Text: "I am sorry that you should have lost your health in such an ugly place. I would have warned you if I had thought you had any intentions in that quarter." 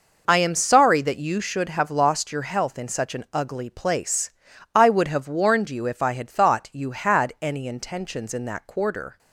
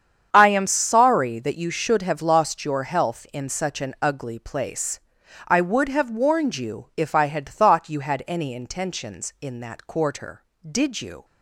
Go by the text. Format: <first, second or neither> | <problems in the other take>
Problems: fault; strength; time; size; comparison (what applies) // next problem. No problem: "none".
first | starts louder than the rest; strong; until 1.3 s; 8 dB // goes on to say "Did you"; from 10.6 s on; 0.56 s long